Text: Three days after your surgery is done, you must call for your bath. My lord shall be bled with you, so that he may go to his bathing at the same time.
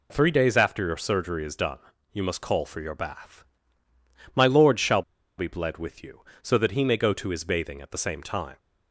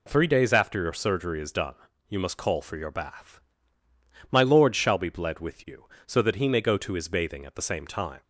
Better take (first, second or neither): second